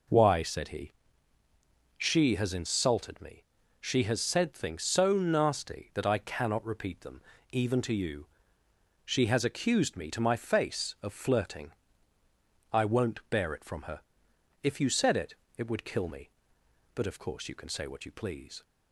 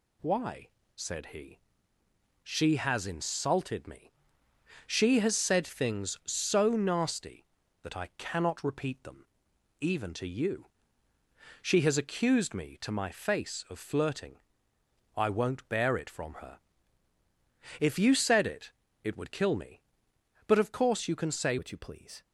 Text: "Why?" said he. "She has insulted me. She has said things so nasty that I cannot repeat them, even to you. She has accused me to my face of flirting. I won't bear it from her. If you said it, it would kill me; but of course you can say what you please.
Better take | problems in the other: first | changes voice at "what"; from 21.5 s on; 0.7 s long

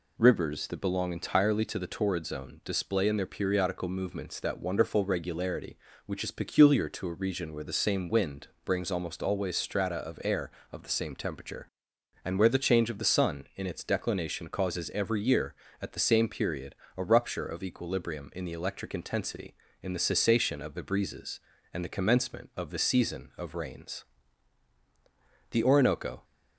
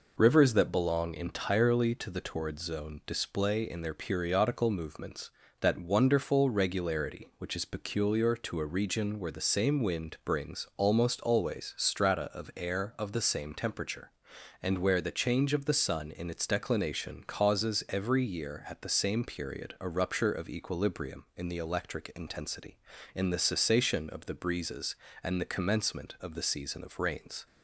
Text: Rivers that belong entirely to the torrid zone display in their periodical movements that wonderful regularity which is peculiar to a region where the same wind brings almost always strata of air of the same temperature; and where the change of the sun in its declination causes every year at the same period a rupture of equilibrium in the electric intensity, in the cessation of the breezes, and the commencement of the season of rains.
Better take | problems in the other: second | pauses between "wind" and "brings"; slight; at 8.4 s; 0.18 s long // pauses between "period" and "a"; slight; at 16.7 s; 0.22 s long // goes on to say "The Orinoco"; noticeable; from 25.5 s on; 0.72 s long

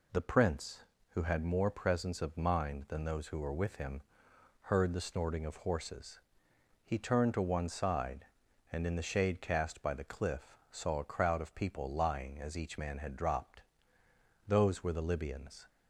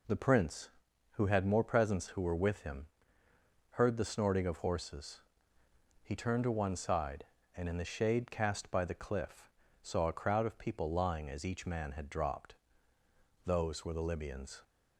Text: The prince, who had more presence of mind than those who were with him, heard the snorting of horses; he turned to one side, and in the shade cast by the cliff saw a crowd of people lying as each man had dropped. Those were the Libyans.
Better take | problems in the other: first | skips "of mind than those"; at 2.0 s // pauses between "cliff" and "saw"; slight; at 9.4 s; 0.36 s long; slight in the first

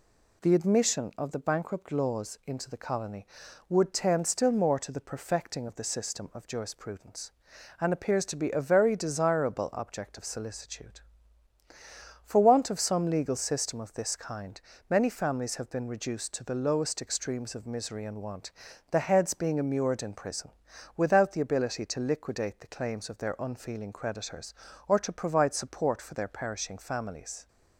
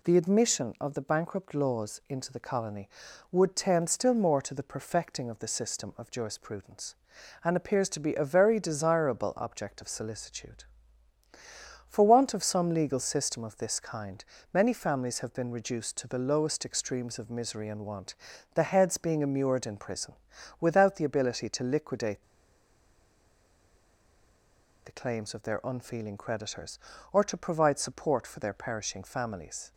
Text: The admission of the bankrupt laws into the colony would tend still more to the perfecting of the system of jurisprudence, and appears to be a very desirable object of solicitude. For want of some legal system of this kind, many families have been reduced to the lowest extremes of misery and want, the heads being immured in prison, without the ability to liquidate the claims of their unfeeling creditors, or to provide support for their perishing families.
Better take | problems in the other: first | pauses between "liquidate" and "the"; strong; at 22.2 s; 2.6 s long

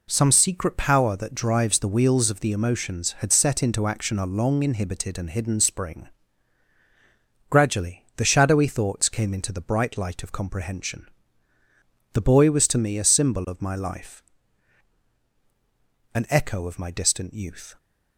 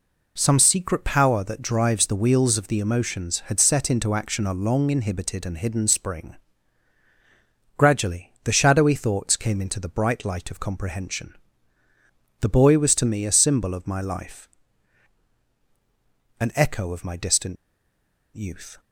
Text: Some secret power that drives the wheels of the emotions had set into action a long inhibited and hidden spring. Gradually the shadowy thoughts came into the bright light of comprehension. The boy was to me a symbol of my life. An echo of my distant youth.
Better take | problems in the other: first | pauses between "distant" and "youth"; noticeable; at 17.5 s; 0.79 s long

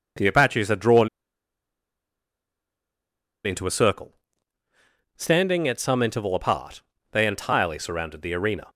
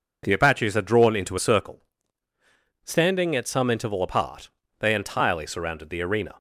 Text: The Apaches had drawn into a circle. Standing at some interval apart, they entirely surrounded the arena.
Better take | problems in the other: second | pauses between "drawn" and "into"; strong; at 1.0 s; 2.3 s long

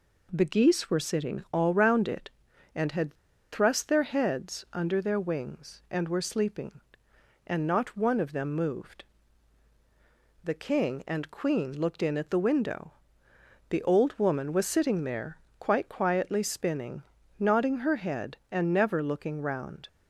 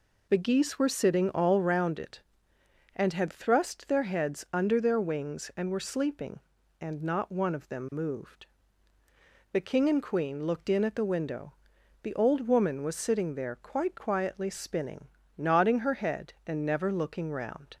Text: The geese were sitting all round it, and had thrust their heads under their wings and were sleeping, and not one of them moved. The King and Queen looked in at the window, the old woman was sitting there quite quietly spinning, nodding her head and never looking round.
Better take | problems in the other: second | pauses between "had" and "thrust"; at 3.1 s; 0.38 s long // pauses between "there" and "quite"; slight; at 15.3 s; 0.20 s long

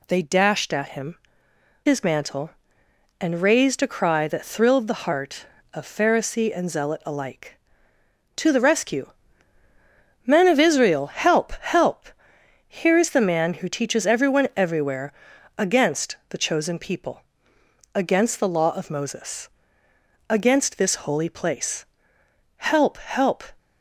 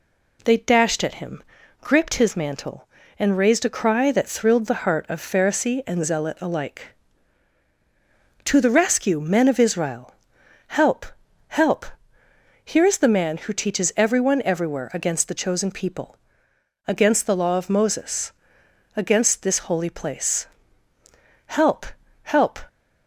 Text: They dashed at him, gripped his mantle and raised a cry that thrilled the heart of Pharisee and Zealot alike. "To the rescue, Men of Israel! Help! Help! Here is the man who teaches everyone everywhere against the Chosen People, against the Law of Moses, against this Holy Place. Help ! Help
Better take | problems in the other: second | skips "gripped"; at 1.5 s // pauses between "everywhere" and "against"; noticeable; at 15.1 s; 0.46 s long

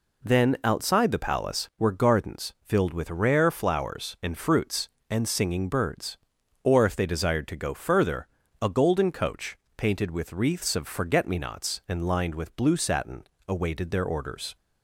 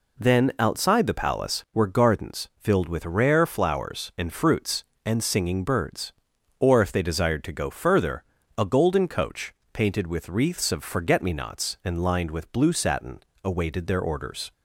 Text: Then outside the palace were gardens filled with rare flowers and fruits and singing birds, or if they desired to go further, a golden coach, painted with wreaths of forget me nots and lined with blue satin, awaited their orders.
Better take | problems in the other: neither | none

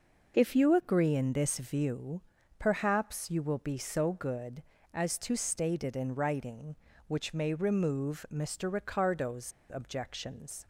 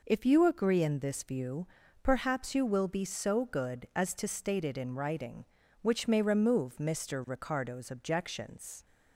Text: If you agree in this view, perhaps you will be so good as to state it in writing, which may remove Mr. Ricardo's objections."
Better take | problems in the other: second | pauses between "Ricardo's" and "objections"; slight; at 9.5 s; 0.21 s long

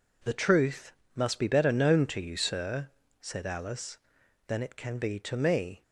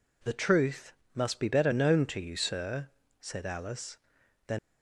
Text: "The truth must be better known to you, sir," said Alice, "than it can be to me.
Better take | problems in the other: first | pauses between "truth" and "must"; slight; at 0.9 s; 0.22 s long; slight in the first // stops before "it can be to me"; at 4.5 s

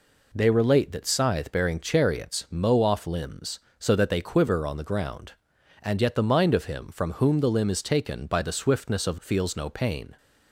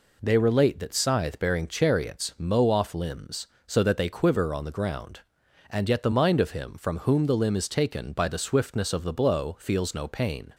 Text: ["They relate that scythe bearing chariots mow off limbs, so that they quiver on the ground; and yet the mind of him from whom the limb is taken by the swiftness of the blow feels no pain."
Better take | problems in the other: second | skips "the blow"; at 9.2 s

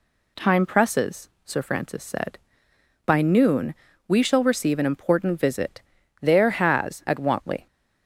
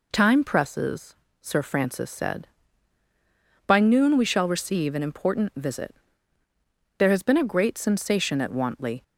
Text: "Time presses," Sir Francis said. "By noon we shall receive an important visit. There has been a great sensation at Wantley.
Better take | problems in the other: second | pauses between "noon" and "we"; slight; at 3.7 s; 0.34 s long // skips "been a great sensation"; at 7.0 s

